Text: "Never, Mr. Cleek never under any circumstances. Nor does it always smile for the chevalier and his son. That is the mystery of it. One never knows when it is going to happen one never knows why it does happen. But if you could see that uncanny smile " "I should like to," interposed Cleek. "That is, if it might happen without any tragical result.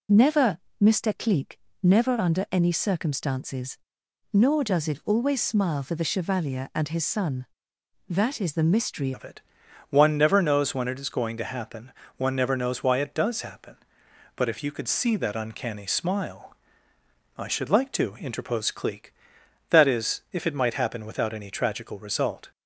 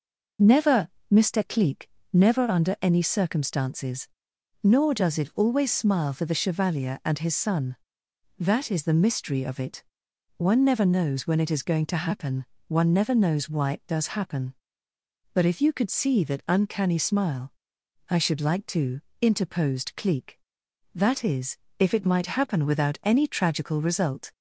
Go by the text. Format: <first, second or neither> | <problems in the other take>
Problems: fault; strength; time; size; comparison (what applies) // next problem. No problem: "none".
second | pauses between "Cleek" and "never"; slight; at 1.6 s; 0.24 s long; slight in the second // changes voice at "of"; from 9.1 s on; 13.4 s long // pauses between "happen" and "one"; slight; at 11.9 s; 0.26 s long; slight in the second